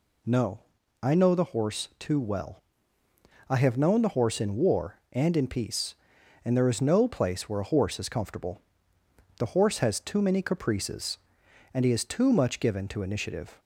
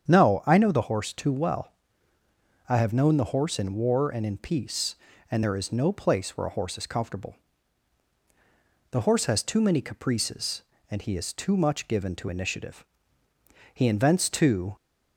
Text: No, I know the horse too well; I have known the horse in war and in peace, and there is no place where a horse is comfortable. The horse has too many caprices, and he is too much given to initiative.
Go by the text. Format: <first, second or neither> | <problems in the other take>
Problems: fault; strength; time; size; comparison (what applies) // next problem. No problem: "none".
first | starts louder than the rest; strong; until 1.1 s; 8 dB // goes on to say "He invents too"; noticeable; from 13.7 s on; 1.0 s long